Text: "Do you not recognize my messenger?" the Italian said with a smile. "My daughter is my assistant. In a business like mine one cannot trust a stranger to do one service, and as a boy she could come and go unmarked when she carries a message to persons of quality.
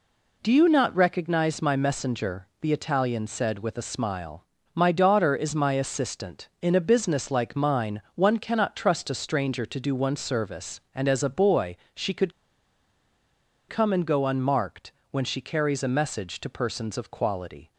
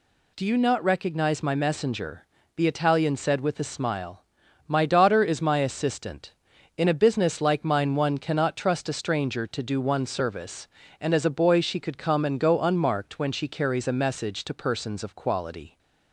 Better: second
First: pauses between "boy" and "she"; slight; at 11.7 s; 0.18 s long // pauses between "could" and "come"; strong; at 12.3 s; 1.3 s long // pauses between "unmarked" and "when"; slight; at 14.9 s; 0.18 s long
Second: none

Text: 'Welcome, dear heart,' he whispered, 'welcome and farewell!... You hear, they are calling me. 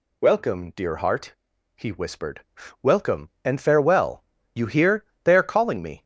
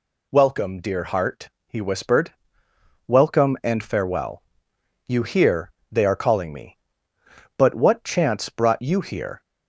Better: first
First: none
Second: goes on to say "But what chance brought you here"; strong; from 7.5 s on; 1.8 s long

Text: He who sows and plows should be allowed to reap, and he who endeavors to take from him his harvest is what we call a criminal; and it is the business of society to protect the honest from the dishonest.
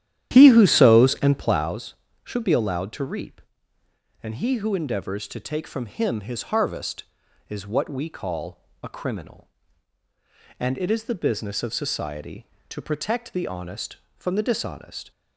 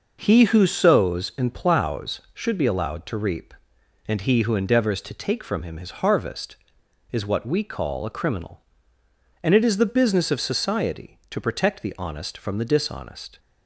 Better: second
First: starts louder than the rest; strong; until 1.7 s; 11.5 dB // pauses between "call" and "a"; slight; at 8.6 s; 0.20 s long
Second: none

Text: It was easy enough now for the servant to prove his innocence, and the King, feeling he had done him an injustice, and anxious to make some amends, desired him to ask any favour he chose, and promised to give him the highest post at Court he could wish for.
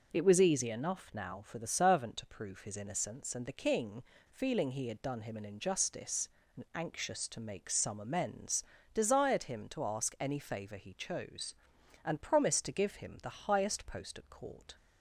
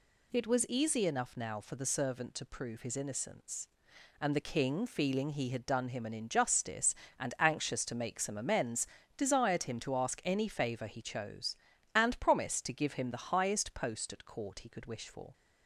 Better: second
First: stops before "he could wish for"; at 14.7 s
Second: none

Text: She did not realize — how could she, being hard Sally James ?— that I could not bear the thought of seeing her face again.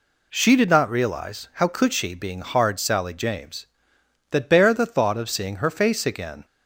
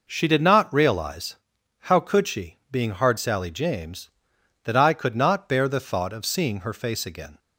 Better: second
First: skips "I could not"; at 4.4 s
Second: none

